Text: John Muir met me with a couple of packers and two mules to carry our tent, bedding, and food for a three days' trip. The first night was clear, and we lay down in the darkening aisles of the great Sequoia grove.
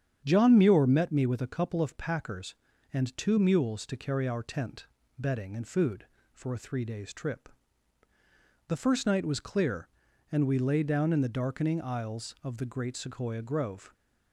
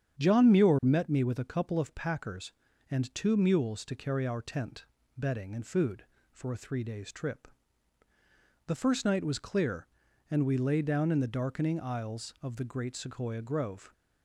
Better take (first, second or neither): neither